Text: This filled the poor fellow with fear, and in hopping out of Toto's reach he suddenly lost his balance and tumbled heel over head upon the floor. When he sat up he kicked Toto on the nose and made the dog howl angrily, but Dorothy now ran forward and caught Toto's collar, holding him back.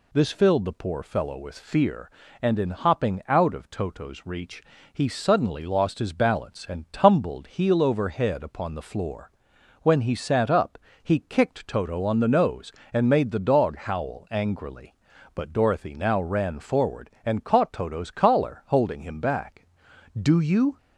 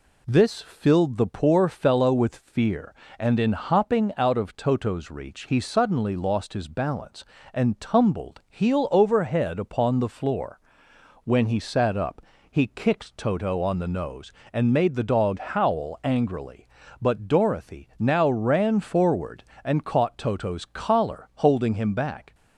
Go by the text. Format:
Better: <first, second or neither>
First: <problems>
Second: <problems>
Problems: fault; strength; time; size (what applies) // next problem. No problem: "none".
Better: second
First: pauses between "reach" and "he"; slight; at 4.6 s; 0.32 s long // pauses between "up" and "he"; slight; at 10.7 s; 0.24 s long // goes on to say "Do you"; from 20.1 s on; 0.58 s long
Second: pauses between "up" and "he"; slight; at 12.2 s; 0.24 s long